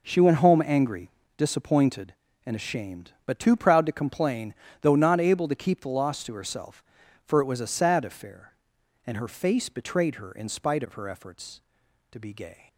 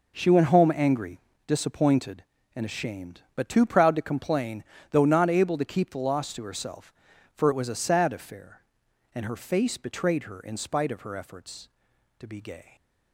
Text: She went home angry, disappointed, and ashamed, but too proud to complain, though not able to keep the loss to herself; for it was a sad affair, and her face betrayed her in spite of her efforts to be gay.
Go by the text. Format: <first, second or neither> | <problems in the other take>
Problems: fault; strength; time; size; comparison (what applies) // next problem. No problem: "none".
neither | none